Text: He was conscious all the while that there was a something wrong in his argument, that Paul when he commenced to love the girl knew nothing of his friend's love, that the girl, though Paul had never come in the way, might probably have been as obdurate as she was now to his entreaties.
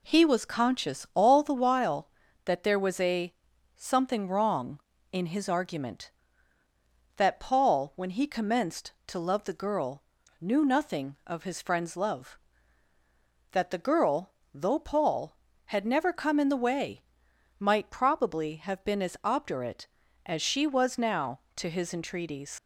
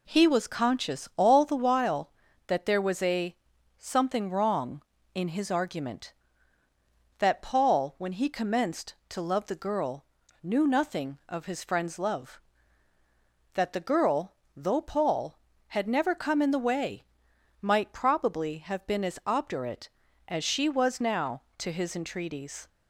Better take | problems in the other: second | pauses between "a" and "something"; at 3.3 s; 0.42 s long; also in the second // pauses between "girl" and "knew"; at 10.0 s; 0.40 s long; also in the second // leaves "entreaties" unfinished; at 22.5 s; 75 ms

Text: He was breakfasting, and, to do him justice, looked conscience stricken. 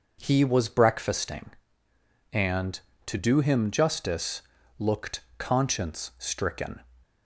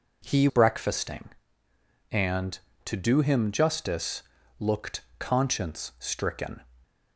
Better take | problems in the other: first | skips "was"; at 0.4 s // pauses between "looked" and "conscience"; slight; at 5.0 s; 0.18 s long; slight in the first

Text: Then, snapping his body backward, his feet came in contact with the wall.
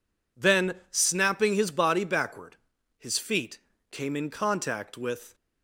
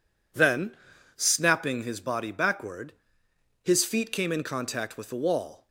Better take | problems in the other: second | pauses between "feet" and "came"; slight; at 3.5 s; 0.30 s long // stops before "the wall"; at 5.3 s

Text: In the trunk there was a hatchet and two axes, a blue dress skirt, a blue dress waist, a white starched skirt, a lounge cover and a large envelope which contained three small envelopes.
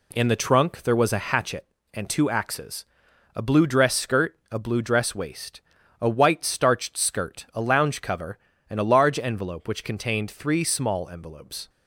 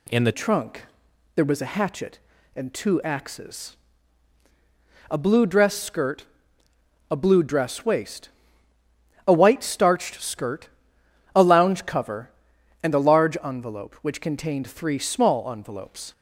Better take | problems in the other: first | changes voice at "trunk"; from 0.3 s on; 15.8 s long // pauses between "trunk" and "there"; noticeable; at 0.8 s; 0.52 s long

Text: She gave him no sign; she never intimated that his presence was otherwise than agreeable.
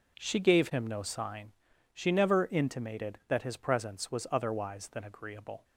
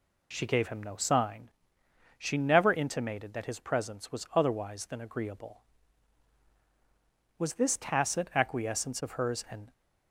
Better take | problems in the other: first | goes on to say "Was this tacit acquiescence of hers an"; strong; from 7.3 s on; 2.3 s long

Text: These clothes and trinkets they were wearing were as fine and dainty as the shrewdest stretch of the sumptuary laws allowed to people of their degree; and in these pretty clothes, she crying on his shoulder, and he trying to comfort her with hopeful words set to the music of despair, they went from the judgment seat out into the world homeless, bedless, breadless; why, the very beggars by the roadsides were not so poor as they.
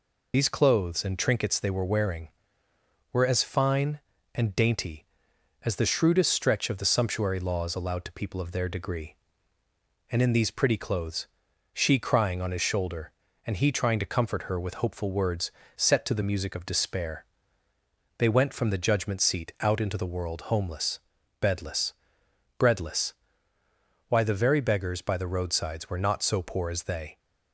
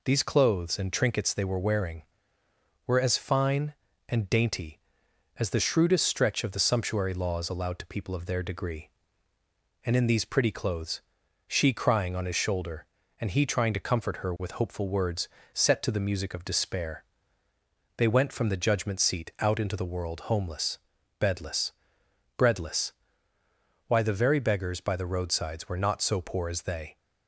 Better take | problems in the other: second | loses the start of "These"; at 0.3 s; 45 ms // pauses between "words" and "set"; slight; at 15.4 s; 0.28 s long; slight in the second

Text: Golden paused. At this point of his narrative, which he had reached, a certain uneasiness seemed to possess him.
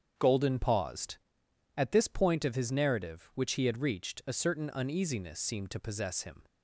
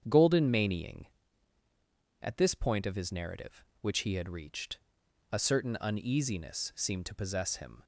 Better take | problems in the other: first | starts louder than the rest; strong; until 2.2 s; 8 dB; strong in the first // says "manying" for "paused"; at 0.4 s

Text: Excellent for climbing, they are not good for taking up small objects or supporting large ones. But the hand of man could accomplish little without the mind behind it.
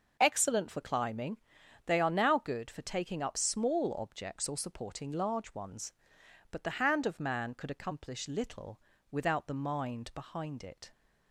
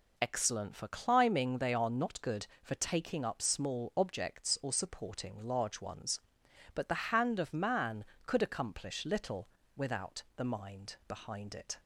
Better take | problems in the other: second | says "now" for "not"; at 2.0 s // pauses between "little" and "without"; slight; at 8.7 s; 0.32 s long; slight in the second

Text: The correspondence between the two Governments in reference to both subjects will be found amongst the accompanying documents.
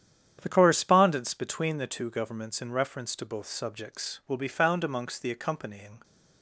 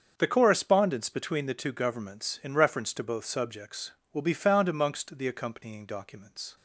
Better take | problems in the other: second | starts louder than the rest; strong; until 1.4 s; 9 dB; also in the second // stops before "documents"; at 6.0 s

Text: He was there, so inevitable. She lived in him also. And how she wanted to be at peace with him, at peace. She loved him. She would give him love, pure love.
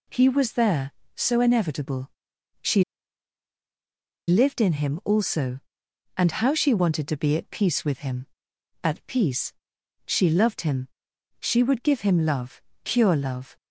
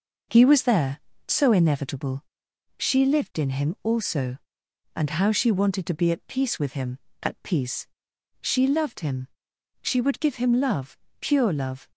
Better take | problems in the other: second | pauses between "She" and "lived"; strong; at 2.8 s; 1.4 s long

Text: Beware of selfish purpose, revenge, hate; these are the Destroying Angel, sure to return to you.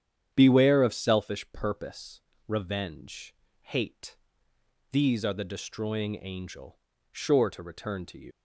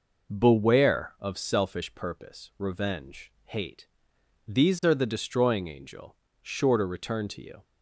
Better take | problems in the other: second | starts louder than the rest; strong; until 1.3 s; 9 dB // leaves "you" unfinished; at 8.3 s; 95 ms

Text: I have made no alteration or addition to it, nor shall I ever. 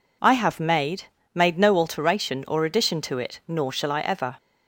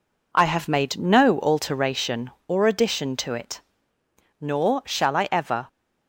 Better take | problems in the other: second | says "made" twice; at 1.3 s

